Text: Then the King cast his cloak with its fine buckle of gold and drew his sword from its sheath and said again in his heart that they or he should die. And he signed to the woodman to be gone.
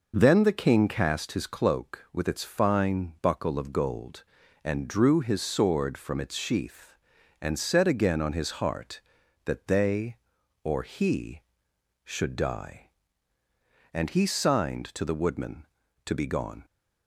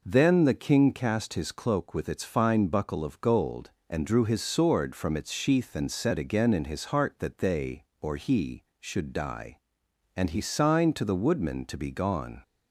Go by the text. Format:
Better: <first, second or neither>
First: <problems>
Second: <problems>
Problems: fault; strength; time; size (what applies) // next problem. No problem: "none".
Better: second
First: says "on" for "in"; at 8.2 s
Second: none